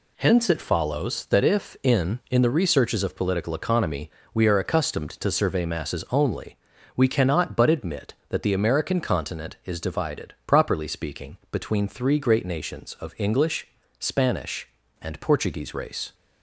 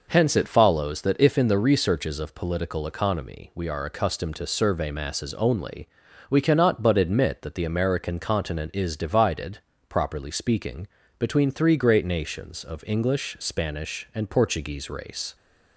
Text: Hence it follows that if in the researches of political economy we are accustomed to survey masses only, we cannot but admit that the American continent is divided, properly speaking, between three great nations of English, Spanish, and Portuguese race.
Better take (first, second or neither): second